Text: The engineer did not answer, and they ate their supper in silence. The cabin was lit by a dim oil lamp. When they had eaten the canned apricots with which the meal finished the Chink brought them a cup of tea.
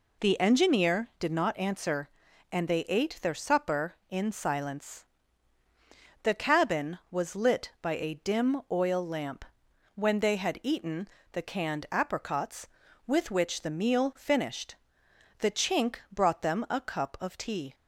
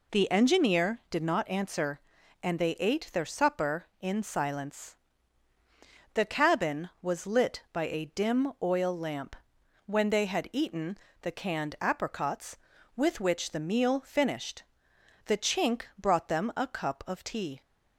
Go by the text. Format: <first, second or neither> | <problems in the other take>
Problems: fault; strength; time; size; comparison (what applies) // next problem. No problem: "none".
neither | pauses between "eaten" and "the"; slight; the same in both // pauses between "finished" and "the"; noticeable; the same in both // pauses between "Chink" and "brought"; slight; the same in both